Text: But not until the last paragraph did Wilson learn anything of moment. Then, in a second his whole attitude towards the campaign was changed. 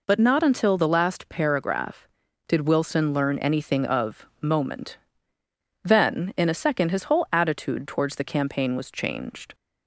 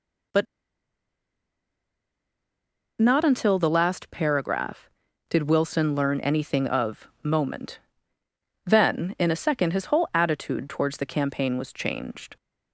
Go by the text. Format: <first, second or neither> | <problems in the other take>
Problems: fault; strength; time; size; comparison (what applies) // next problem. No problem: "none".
first | pauses between "But" and "not"; strong; at 0.4 s; 2.5 s long